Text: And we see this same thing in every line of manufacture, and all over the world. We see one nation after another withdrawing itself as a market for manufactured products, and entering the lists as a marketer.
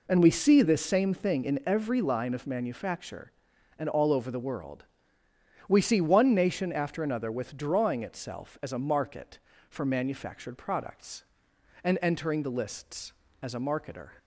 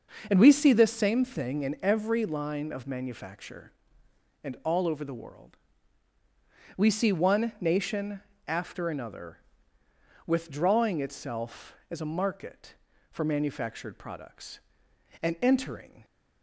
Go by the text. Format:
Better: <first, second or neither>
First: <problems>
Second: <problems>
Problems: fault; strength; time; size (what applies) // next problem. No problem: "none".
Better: first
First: none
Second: pauses between "nation" and "after"; slight; at 8.2 s; 0.26 s long // pauses between "another" and "withdrawing"; noticeable; at 9.3 s; 0.88 s long // stops before "the lists as a marketer"; at 16.0 s